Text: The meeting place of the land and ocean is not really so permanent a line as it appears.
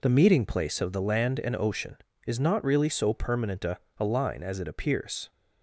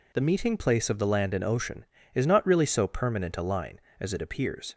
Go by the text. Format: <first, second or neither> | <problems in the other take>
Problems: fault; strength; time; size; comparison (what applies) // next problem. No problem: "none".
second | says "a" twice; at 3.9 s